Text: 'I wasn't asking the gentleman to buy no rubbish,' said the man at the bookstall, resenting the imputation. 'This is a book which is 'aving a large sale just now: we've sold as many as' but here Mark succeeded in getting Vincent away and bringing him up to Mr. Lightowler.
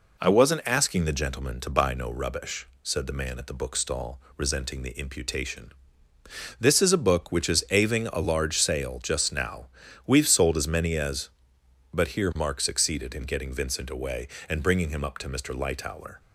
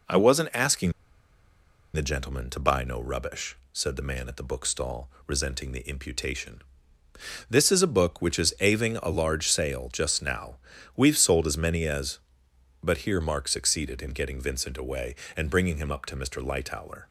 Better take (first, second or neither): first